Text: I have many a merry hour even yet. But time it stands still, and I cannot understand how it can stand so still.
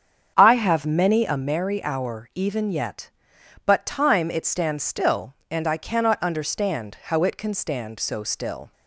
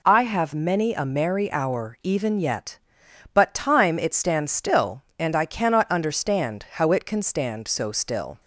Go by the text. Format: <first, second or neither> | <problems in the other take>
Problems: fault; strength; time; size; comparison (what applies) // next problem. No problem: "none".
second | starts louder than the rest; strong; until 1.4 s; 7.5 dB